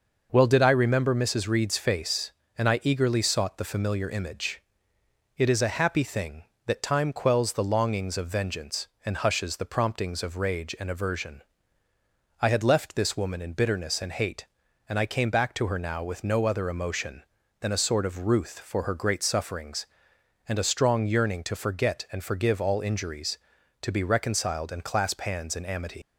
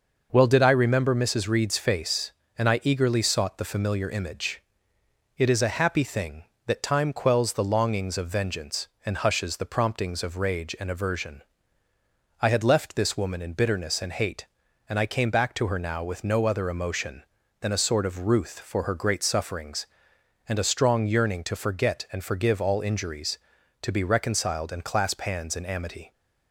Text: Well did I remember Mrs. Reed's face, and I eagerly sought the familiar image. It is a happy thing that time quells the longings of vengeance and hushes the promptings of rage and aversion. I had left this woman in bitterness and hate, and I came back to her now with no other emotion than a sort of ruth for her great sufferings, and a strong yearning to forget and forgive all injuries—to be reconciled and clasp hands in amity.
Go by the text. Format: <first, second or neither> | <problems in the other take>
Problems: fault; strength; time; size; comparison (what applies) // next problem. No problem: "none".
second | leaves "amity" unfinished; at 26.0 s; 100 ms